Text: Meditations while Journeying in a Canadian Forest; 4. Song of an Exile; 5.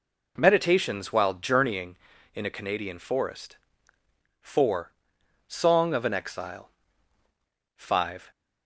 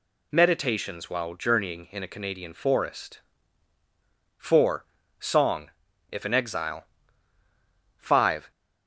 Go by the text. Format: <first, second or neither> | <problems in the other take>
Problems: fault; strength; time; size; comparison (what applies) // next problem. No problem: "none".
first | says "if" for "of"; at 6.1 s